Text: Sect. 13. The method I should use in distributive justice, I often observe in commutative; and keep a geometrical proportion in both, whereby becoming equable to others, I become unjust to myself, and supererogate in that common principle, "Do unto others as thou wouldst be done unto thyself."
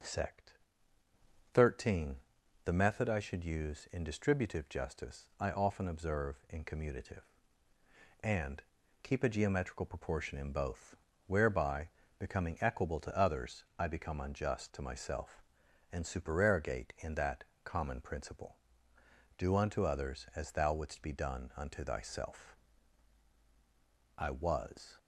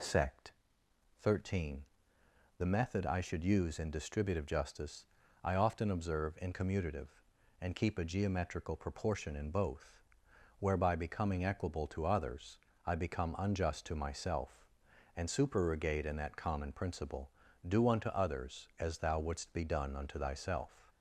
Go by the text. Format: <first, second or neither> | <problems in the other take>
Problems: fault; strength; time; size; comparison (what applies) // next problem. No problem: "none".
second | pauses between "and" and "keep"; at 8.6 s; 0.40 s long // pauses between "whereby" and "becoming"; slight; at 11.8 s; 0.28 s long // pauses between "that" and "common"; slight; at 17.4 s; 0.18 s long // goes on to say "I was"; noticeable; from 24.1 s on; 0.80 s long